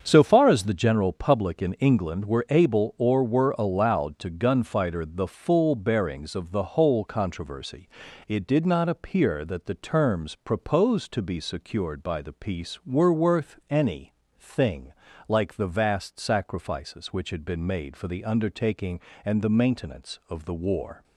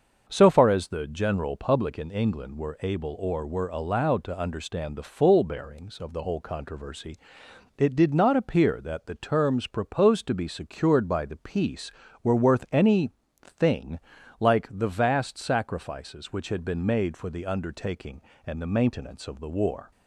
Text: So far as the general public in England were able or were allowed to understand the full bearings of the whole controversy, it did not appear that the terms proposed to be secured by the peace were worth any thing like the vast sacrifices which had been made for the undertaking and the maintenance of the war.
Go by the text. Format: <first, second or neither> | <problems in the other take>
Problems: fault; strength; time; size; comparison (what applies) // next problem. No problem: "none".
second | starts louder than the rest; until 1.0 s; 7 dB; also in the second // says "gunfighter" for "understand"; at 4.3 s // pauses between "any" and "thing"; slight; at 14.1 s; 0.28 s long; slight in the second // pauses between "thing" and "like"; slight; at 14.9 s; 0.36 s long; also in the second